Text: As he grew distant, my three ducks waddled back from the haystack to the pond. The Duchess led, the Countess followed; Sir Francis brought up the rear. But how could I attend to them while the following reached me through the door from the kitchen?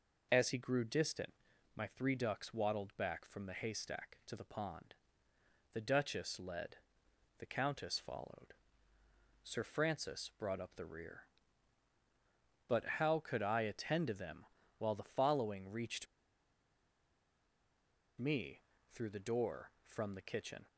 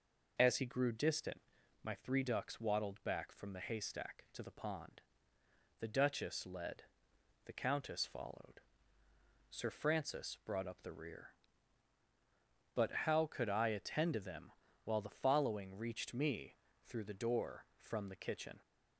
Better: second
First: pauses between "But" and "how"; slight; at 12.8 s; 0.16 s long // pauses between "them" and "while"; slight; at 14.4 s; 0.32 s long // pauses between "reached" and "me"; strong; at 16.0 s; 2.1 s long // pauses between "me" and "through"; slight; at 18.6 s; 0.30 s long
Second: pauses between "But" and "how"; slight; at 12.9 s; 0.16 s long // pauses between "them" and "while"; slight; at 14.5 s; 0.32 s long // pauses between "me" and "through"; slight; at 16.5 s; 0.30 s long

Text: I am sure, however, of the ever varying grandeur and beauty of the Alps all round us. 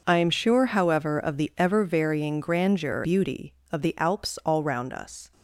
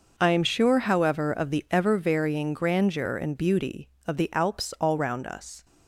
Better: second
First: skips "and"; at 3.0 s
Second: none

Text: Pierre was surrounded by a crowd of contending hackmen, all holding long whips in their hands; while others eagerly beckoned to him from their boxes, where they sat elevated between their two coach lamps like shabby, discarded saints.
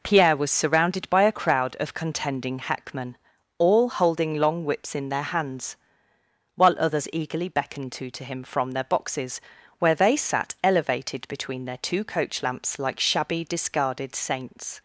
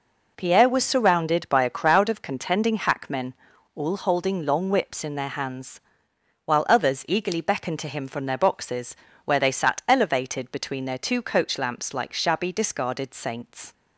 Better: second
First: says "to" twice; at 8.1 s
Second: none

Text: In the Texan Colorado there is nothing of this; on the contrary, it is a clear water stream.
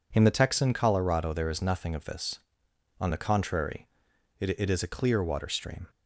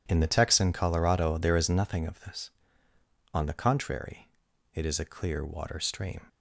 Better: second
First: says "it" twice; at 4.5 s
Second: none

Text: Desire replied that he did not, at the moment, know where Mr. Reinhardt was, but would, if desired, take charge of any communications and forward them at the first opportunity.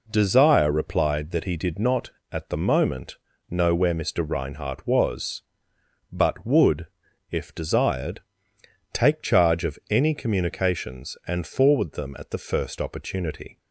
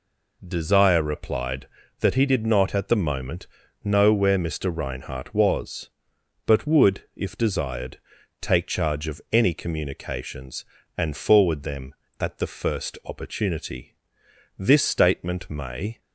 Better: first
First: none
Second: goes on to say "This statement may"; from 14.5 s on; 1.4 s long

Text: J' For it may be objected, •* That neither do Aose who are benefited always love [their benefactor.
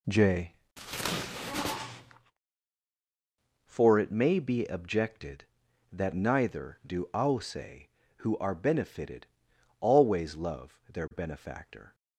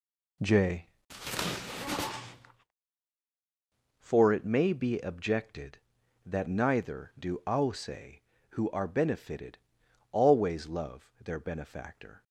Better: neither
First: pauses between "benefited" and "always"; noticeable; at 9.2 s; 0.56 s long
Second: pauses between "benefited" and "always"; noticeable; at 9.5 s; 0.56 s long

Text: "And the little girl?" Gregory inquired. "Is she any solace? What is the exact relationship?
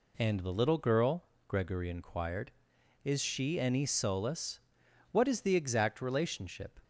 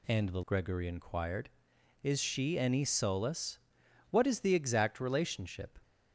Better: first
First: none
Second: skips "little girl"; at 0.4 s

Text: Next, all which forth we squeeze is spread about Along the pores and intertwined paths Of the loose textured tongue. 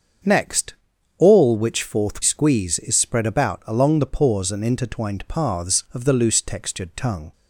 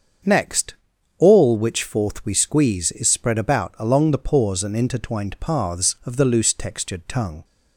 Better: second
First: starts louder than the rest; until 1.6 s; 6.5 dB // skips "we"; at 2.2 s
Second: starts louder than the rest; until 1.6 s; 7 dB

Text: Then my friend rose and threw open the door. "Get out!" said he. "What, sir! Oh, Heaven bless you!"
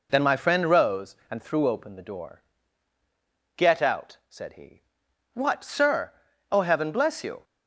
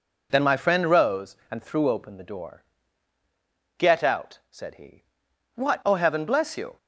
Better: first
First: none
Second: skips "sir"; at 5.8 s

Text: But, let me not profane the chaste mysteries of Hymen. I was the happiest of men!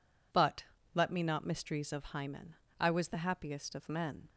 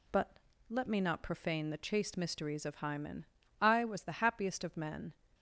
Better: second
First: skips "profane the chaste"; at 1.4 s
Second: none

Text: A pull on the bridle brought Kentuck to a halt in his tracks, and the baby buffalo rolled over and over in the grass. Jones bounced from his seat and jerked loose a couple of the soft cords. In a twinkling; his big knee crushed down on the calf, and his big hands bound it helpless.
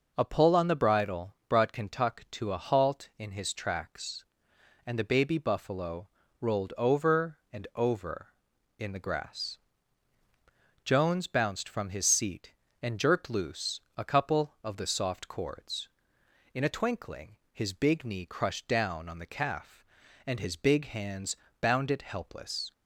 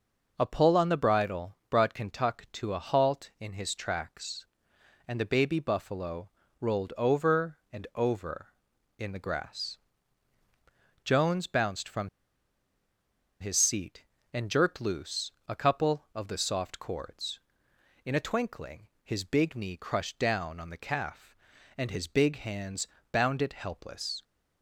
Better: first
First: pauses between "buffalo" and "rolled"; slight; at 6.0 s; 0.33 s long // pauses between "loose" and "a"; slight; at 13.8 s; 0.16 s long // pauses between "hands" and "bound"; slight; at 21.3 s; 0.24 s long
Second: pauses between "buffalo" and "rolled"; slight; at 6.2 s; 0.32 s long // pauses between "from" and "his"; strong; at 12.0 s; 1.3 s long // pauses between "loose" and "a"; slight; at 15.3 s; 0.16 s long // pauses between "hands" and "bound"; slight; at 22.8 s; 0.24 s long

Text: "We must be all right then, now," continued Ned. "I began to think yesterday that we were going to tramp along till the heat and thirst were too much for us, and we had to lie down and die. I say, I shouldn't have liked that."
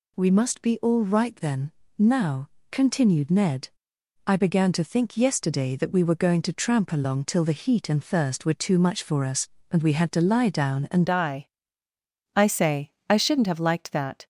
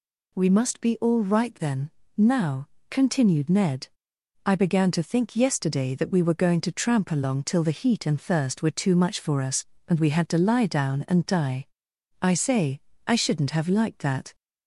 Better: second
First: changes voice at "die"; from 11.0 s on; 3.2 s long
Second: none

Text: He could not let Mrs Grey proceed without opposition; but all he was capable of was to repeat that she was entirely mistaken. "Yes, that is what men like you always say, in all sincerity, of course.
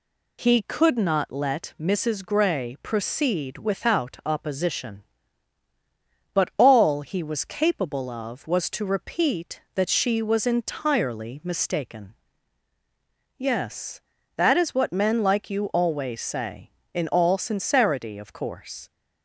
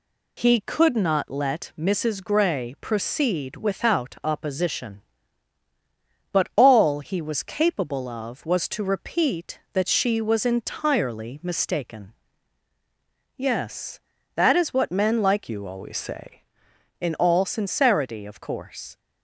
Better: first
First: none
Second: changes voice from "you" to "say"; from 15.4 to 16.4 s; 1.0 s long

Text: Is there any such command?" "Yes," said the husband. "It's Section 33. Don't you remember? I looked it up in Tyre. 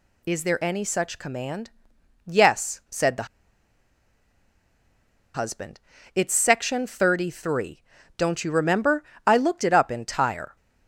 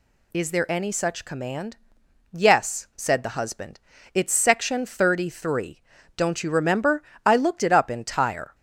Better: second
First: pauses between "the" and "husband"; strong; at 3.2 s; 2.0 s long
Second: none

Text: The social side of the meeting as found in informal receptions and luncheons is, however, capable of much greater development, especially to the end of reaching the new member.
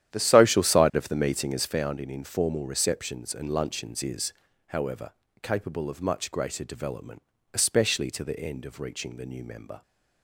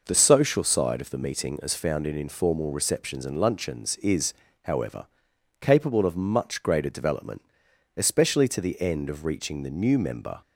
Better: second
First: starts louder than the rest; strong; until 1.8 s; 10.5 dB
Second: none

